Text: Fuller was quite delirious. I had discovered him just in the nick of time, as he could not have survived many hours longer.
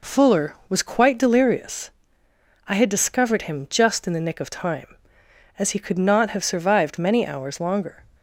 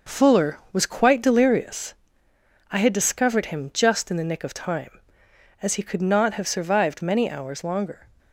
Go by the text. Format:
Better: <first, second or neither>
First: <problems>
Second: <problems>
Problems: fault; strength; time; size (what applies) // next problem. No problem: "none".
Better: first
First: none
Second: gets quieter; throughout; 6.5 dB